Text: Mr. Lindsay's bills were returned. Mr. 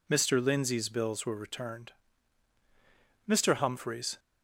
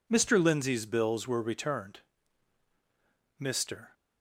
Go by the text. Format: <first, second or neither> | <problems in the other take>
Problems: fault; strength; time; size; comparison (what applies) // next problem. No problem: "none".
second | goes on to say "Humphreys"; noticeable; from 3.5 s on; 0.64 s long